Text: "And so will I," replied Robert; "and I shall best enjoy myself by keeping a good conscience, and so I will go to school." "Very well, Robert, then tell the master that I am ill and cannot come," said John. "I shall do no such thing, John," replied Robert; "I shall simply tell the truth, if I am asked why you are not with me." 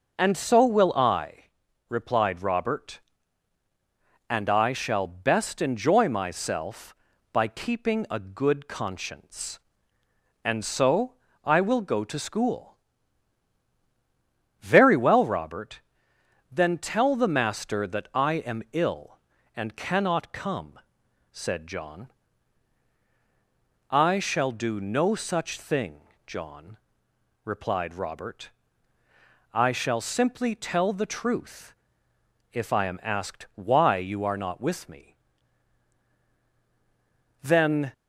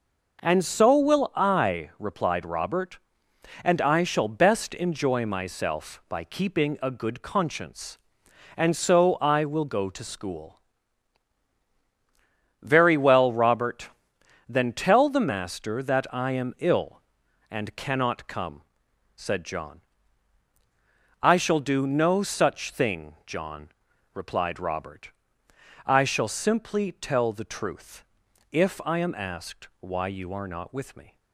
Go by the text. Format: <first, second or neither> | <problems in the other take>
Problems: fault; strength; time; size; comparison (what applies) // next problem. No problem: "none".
second | pauses between "so" and "I"; slight; at 11.1 s; 0.30 s long // goes on to say "Then"; from 37.4 s on; 0.52 s long